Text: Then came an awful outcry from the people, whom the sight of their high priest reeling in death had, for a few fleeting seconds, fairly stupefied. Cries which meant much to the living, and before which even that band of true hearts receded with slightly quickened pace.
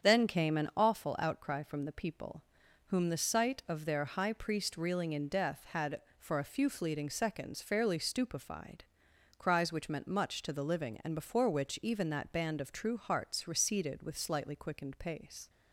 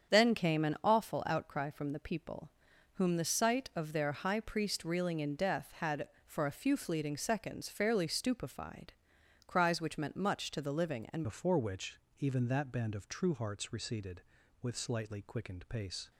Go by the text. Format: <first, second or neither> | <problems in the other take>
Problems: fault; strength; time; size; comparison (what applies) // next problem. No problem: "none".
first | starts louder than the rest; strong; until 1.1 s; 8 dB; strong in the first // changes voice at "before"; from 11.2 s on; 4.9 s long // pauses between "which" and "even"; slight; at 11.9 s; 0.20 s long